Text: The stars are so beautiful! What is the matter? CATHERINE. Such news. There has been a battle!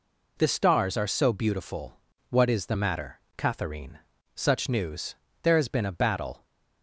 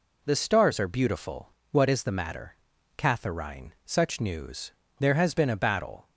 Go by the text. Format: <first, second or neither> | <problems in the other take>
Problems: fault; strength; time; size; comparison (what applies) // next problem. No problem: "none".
first | skips "so"; at 0.8 s